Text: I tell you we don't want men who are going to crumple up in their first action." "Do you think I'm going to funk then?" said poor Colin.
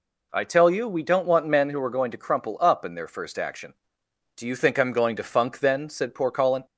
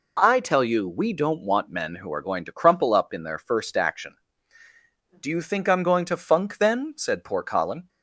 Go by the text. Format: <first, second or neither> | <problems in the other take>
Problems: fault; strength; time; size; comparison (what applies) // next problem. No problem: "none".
neither | none